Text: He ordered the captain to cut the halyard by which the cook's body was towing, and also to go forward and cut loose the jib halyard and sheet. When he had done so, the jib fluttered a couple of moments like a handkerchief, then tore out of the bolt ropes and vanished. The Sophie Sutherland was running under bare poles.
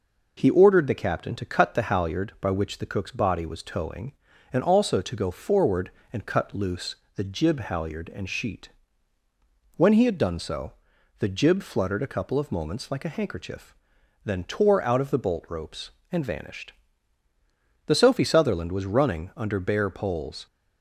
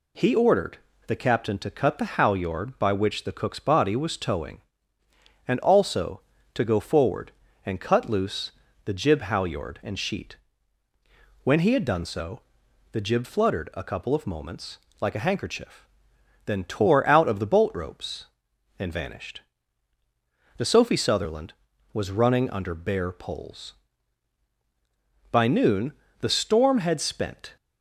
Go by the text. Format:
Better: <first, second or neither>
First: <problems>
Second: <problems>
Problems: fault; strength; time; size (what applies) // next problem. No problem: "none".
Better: first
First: pauses between "loose" and "the"; slight; at 6.9 s; 0.22 s long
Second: pauses between "ordered" and "the"; slight; at 0.7 s; 0.30 s long // pauses between "loose" and "the"; slight; at 8.5 s; 0.36 s long // pauses between "moments" and "like"; slight; at 14.7 s; 0.24 s long // goes on to say "By noon the storm had spent"; strong; from 25.3 s on; 2.2 s long